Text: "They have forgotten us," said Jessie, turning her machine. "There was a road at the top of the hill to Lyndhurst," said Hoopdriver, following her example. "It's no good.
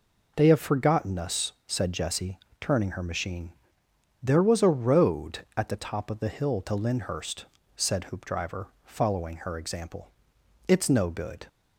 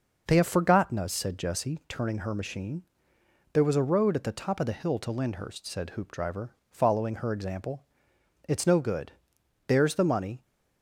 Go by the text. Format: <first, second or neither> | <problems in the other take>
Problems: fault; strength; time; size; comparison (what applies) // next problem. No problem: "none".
first | goes on to say "There's the money"; noticeable; from 9.6 s on; 0.74 s long